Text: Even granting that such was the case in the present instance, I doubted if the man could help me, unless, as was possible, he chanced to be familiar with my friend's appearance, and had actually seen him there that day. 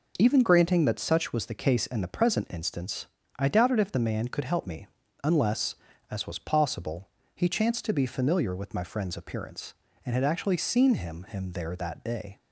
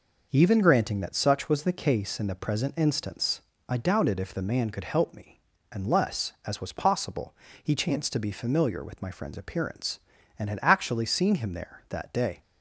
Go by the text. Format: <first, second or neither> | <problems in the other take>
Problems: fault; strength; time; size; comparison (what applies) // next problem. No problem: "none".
second | says "him" twice; at 11.2 s